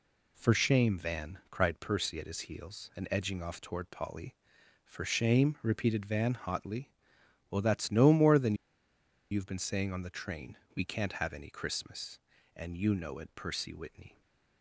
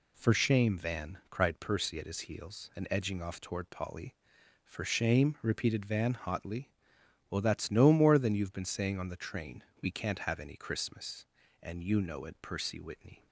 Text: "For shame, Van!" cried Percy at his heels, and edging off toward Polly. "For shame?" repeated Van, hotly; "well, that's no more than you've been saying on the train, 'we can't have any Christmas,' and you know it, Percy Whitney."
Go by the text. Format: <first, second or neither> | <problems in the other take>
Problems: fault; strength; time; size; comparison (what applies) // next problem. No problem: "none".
second | pauses between "than" and "you've"; noticeable; at 8.5 s; 0.77 s long // stays silent after the last word; slight; from 14.0 s on; 0.6 s long